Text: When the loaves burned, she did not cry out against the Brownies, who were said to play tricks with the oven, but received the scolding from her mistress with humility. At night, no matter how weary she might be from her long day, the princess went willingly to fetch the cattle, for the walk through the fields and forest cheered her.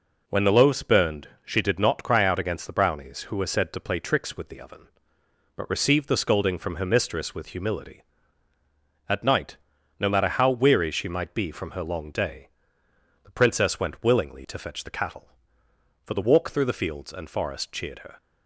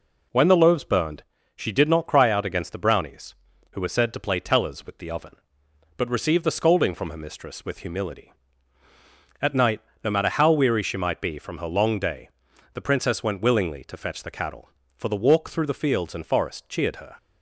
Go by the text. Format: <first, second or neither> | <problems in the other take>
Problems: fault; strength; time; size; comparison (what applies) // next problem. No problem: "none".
first | says "tellers" for "tricks"; at 4.3 s